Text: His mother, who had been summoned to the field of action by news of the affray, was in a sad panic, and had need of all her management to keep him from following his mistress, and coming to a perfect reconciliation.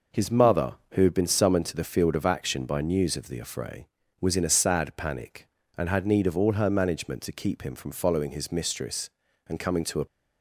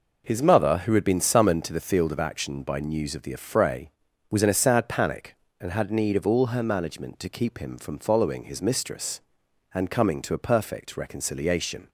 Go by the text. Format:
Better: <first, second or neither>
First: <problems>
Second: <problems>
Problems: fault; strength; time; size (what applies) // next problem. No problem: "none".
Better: second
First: stops before "perfect reconciliation"; at 10.0 s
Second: none